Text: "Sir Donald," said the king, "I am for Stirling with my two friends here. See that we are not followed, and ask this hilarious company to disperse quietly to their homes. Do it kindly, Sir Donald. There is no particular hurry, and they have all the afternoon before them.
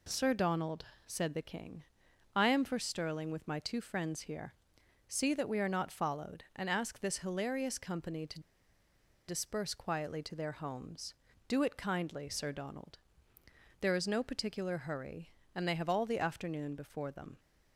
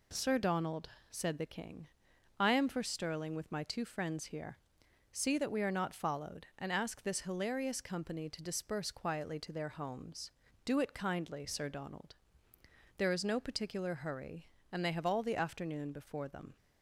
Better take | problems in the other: second | pauses between "to" and "disperse"; noticeable; at 8.3 s; 0.88 s long

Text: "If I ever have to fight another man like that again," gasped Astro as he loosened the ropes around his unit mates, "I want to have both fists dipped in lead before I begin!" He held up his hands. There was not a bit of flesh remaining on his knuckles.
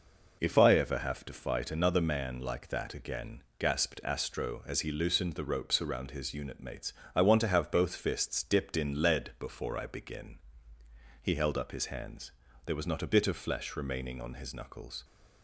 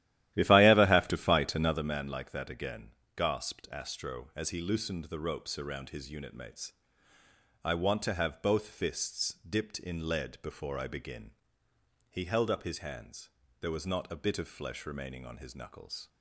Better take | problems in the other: first | starts louder than the rest; strong; until 1.8 s; 13.5 dB

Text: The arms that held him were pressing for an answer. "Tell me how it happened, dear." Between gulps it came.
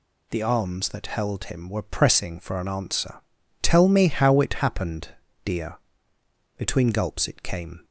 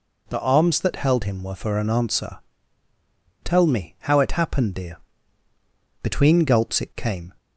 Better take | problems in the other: first | skips "pressing"; at 1.5 s

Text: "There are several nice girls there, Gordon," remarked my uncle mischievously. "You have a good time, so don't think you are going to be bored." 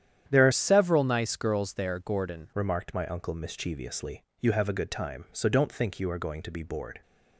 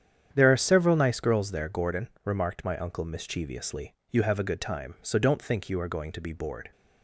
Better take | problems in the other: second | starts louder than the rest; strong; until 1.2 s; 10 dB; strong in the second // changes voice from "several" to "Gordon"; from 0.5 to 2.4 s; 1.9 s long

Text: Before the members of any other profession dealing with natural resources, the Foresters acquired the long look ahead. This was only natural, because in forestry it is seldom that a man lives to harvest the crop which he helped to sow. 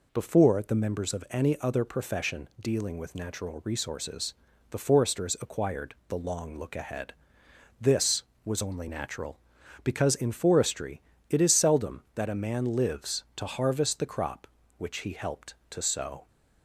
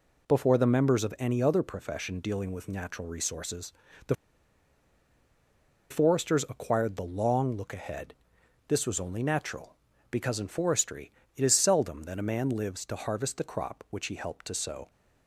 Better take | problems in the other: first | pauses between "the" and "Foresters"; strong; at 4.1 s; 1.7 s long // pauses between "forestry" and "it"; slight; at 11.1 s; 0.24 s long; slight in the first

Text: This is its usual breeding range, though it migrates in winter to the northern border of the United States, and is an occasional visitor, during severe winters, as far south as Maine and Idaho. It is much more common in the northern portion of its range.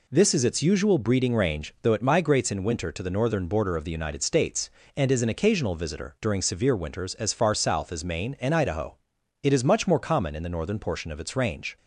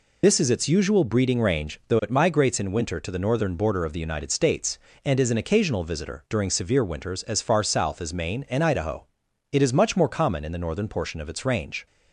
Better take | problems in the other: first | loses the start of "This"; at 0.2 s; 85 ms

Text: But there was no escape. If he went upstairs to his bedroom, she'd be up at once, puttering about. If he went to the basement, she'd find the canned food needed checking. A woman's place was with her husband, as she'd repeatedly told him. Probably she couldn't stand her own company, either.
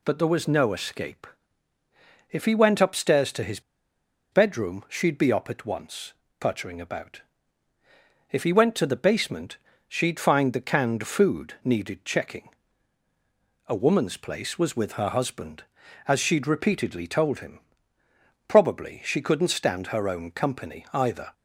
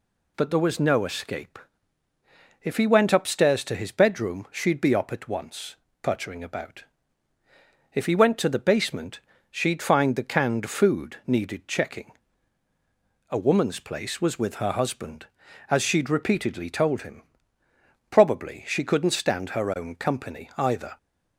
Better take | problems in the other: second | pauses between "his" and "bedroom"; noticeable; at 3.5 s; 0.72 s long

